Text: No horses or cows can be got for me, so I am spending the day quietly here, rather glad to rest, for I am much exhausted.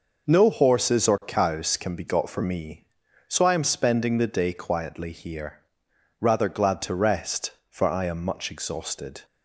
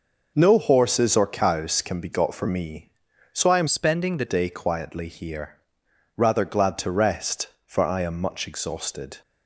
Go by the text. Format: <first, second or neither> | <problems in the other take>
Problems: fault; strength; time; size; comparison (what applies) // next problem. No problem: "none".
first | changes voice from "spending" to "the"; from 3.6 to 4.2 s; 0.6 s long